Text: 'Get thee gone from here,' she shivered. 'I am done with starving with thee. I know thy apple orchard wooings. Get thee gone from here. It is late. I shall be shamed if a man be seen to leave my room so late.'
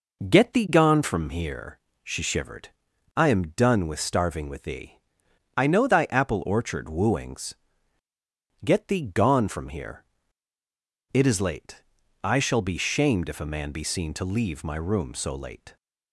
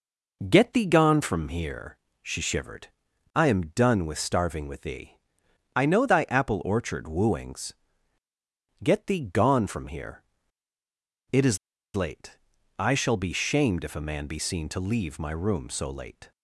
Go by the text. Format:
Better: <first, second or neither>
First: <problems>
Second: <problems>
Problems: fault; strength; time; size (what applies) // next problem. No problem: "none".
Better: first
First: none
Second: pauses between "is" and "late"; at 11.5 s; 0.37 s long